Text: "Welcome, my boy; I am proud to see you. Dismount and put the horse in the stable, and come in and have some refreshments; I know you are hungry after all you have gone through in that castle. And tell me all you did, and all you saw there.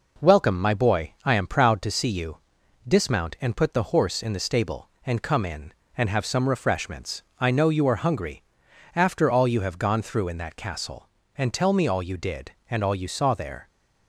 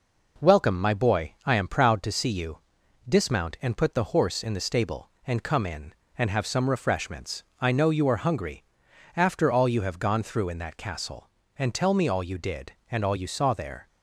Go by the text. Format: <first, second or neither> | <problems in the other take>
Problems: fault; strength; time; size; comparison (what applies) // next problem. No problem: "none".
neither | pauses between "hungry" and "after"; noticeable; the same in both